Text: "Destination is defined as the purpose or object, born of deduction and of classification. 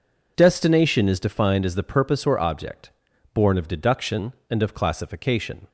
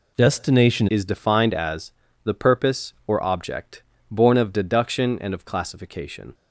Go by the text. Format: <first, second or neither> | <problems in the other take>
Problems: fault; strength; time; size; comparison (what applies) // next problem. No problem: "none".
first | changes voice at "is"; from 0.8 s on; 5.5 s long // pauses between "as" and "the"; slight; at 1.9 s; 0.32 s long